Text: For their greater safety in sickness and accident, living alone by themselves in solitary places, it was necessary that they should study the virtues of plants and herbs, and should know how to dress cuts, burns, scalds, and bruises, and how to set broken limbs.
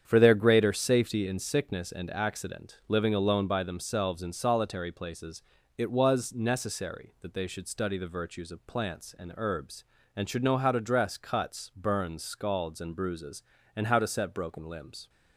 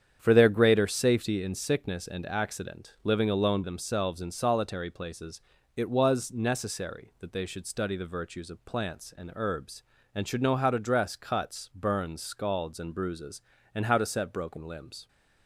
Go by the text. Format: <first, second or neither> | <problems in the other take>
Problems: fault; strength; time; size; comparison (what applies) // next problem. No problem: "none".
first | starts louder than the rest; strong; until 1.2 s; 8.5 dB; strong in the first // skips "by"; at 3.6 s